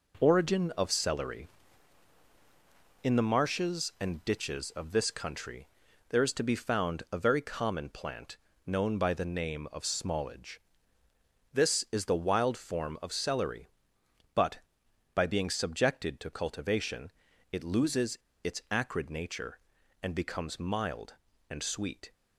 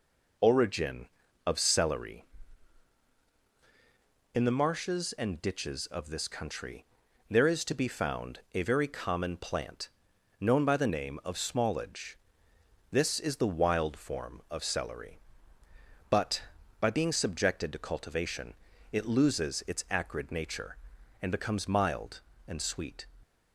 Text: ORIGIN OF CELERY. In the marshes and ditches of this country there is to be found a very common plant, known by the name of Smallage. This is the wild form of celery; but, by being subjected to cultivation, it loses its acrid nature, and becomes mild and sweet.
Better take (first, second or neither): second